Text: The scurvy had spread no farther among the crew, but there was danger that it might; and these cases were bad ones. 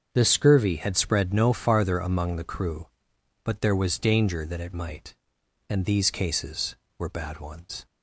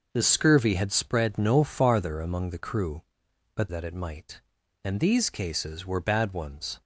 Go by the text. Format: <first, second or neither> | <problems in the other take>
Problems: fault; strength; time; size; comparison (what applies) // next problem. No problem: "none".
first | starts louder than the rest; noticeable; until 1.1 s; 6 dB; also in the first // skips "there was danger"; at 3.6 s